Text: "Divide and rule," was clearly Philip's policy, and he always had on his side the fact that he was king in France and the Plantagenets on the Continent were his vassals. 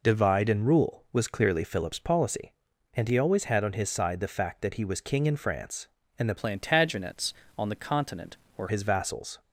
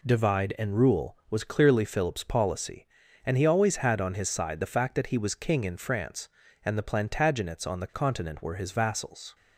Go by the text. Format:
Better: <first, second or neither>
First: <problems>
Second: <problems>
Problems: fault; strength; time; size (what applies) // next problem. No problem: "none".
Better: second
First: changes voice from "Plantagenets" to "were"; from 6.3 to 8.6 s; 2.3 s long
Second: none